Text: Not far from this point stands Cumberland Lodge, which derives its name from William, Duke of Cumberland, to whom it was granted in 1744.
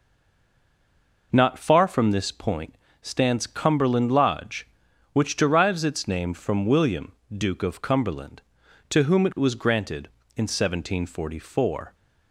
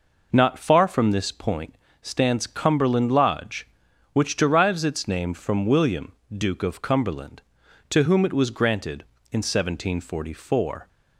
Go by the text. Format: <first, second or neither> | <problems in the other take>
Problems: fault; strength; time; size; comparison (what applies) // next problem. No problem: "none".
second | stays silent before the first word; noticeable; until 1.3 s; 1.3 s long // pauses between "point" and "stands"; slight; at 2.7 s; 0.28 s long; slight in the second